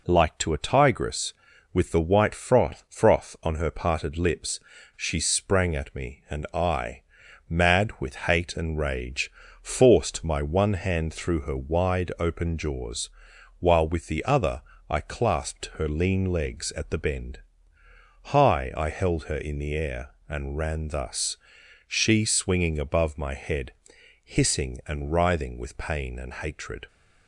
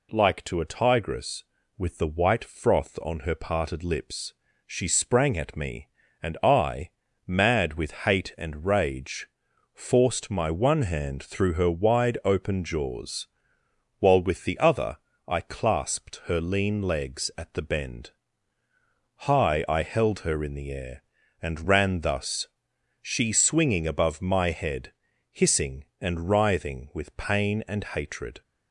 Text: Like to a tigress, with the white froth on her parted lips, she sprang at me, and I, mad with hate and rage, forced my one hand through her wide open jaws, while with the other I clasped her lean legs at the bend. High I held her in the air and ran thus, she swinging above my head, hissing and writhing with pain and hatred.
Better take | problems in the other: second | says "froth" twice; at 2.8 s // pauses between "other" and "I"; slight; at 14.6 s; 0.26 s long; slight in the second

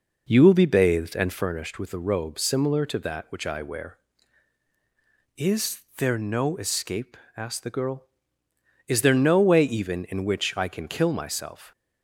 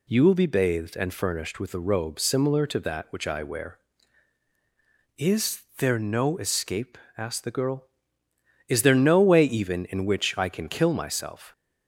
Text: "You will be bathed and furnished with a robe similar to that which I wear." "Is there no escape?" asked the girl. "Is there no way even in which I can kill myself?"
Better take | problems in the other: second | starts louder than the rest; noticeable; until 1.5 s; 5 dB // pauses between "Is" and "there"; slight; at 5.8 s; 0.16 s long; slight in the second

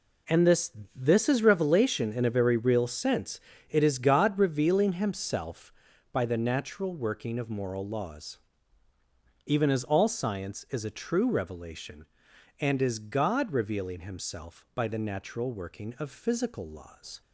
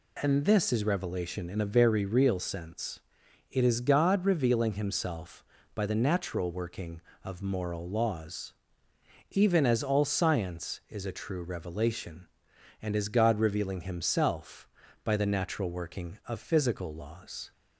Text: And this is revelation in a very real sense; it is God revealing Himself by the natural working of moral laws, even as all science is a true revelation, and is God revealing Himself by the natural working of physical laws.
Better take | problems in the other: second | says "this" twice; at 0.9 s

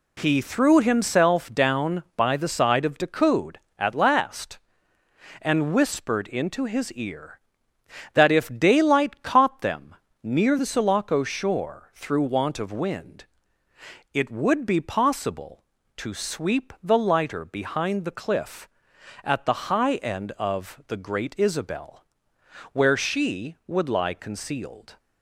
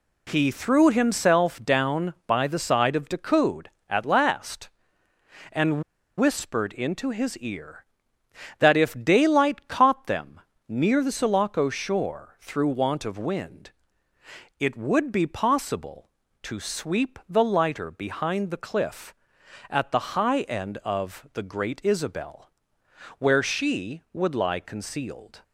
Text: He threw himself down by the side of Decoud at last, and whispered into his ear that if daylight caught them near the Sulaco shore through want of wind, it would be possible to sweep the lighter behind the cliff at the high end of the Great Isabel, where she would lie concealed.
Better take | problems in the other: first | pauses between "and" and "whispered"; at 5.8 s; 0.37 s long // pauses between "them" and "near"; slight; at 10.3 s; 0.30 s long; slight in the first

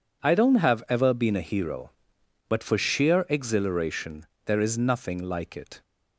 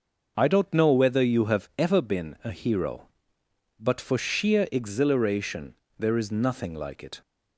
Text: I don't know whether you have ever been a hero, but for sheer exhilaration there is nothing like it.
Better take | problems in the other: second | skips "know whether you"; at 0.5 s // pauses between "exhilaration" and "there"; slight; at 4.2 s; 0.20 s long; slight in the second

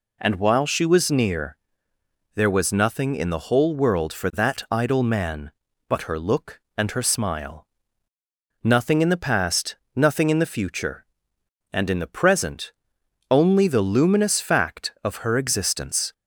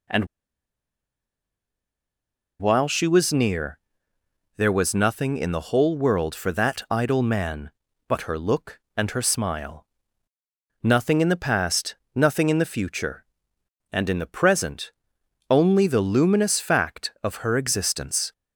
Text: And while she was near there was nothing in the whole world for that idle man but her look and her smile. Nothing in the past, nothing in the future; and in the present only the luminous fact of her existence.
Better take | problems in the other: first | pauses between "And" and "while"; strong; at 0.2 s; 2.3 s long // pauses between "near" and "there"; noticeable; at 3.7 s; 0.78 s long; noticeable in the first // pauses between "present" and "only"; noticeable; at 14.9 s; 0.58 s long; noticeable in the first

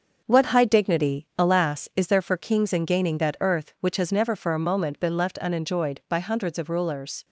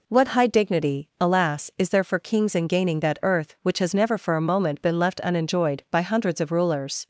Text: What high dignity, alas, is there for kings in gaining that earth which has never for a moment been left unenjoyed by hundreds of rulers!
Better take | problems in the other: second | gets quieter; noticeable; throughout; 5 dB

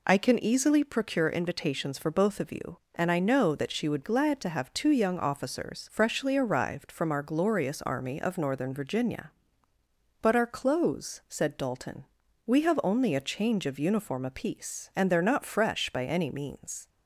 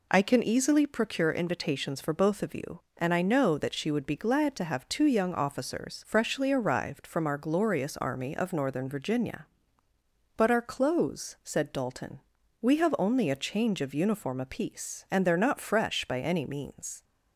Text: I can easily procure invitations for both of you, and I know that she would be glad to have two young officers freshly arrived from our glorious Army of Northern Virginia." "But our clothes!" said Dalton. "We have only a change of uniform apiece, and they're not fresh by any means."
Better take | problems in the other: second | skips "be"; at 4.0 s

